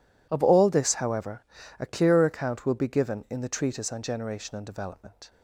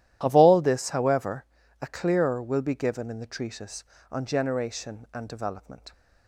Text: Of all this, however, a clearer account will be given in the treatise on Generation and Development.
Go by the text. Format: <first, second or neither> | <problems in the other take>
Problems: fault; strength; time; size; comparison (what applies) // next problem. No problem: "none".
first | starts louder than the rest; strong; until 1.2 s; 12.5 dB // skips "account"; at 2.4 s